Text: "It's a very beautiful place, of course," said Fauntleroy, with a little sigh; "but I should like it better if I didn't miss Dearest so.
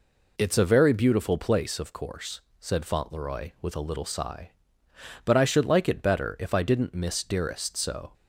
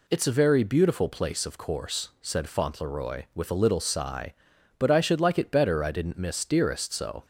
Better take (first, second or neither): first